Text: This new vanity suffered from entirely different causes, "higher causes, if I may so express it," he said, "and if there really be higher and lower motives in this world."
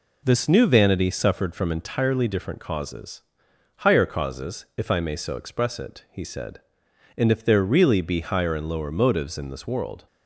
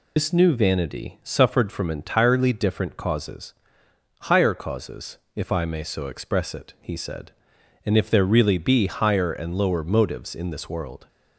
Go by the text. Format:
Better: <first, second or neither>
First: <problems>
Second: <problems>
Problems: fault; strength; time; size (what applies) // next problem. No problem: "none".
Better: first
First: none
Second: loses the start of "This"; at 0.1 s; 120 ms